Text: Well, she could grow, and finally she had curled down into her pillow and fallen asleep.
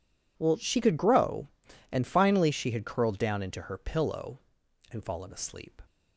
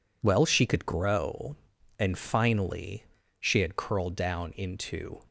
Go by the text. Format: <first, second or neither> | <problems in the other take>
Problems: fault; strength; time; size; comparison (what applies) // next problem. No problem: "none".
first | pauses between "finally" and "she"; slight; at 3.0 s; 0.34 s long // stops before "her pillow and fallen asleep"; at 5.2 s